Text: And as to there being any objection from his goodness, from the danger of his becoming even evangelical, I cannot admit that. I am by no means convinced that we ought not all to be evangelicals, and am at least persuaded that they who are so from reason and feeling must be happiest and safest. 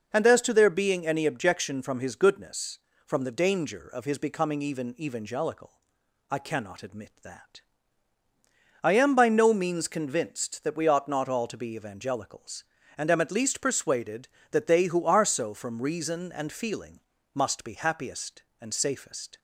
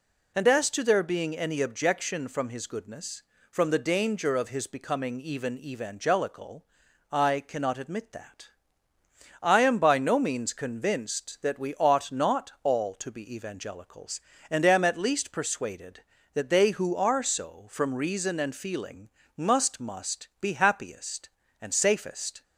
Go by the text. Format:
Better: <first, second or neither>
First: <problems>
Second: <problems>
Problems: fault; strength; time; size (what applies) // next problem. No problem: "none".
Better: first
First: pauses between "feeling" and "must"; slight; at 17.0 s; 0.34 s long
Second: pauses between "feeling" and "must"; slight; at 19.0 s; 0.28 s long // says "must" twice; at 19.8 s